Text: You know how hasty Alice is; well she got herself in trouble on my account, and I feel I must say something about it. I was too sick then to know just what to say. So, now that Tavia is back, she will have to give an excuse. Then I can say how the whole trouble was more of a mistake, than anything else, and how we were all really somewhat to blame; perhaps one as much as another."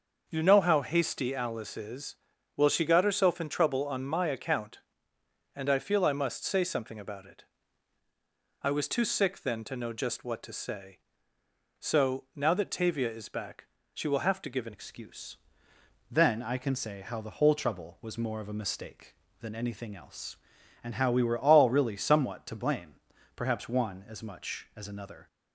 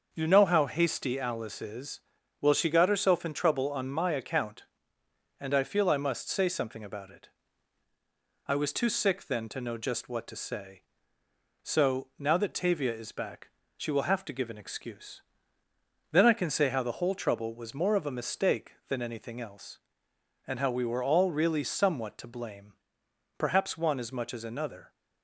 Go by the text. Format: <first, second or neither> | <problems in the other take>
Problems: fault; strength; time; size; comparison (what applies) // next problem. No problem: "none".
second | starts louder than the rest; until 1.2 s; 6.5 dB; also in the second // changes voice at "excuse"; from 14.7 s on; 10.5 s long